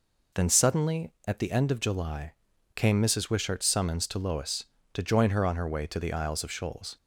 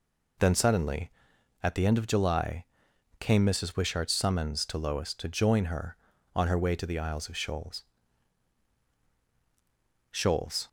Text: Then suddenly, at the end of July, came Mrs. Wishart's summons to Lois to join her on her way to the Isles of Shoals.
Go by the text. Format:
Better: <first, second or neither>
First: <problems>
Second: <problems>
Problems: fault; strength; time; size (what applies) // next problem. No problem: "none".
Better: first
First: none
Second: says "Shoals" twice; at 10.1 s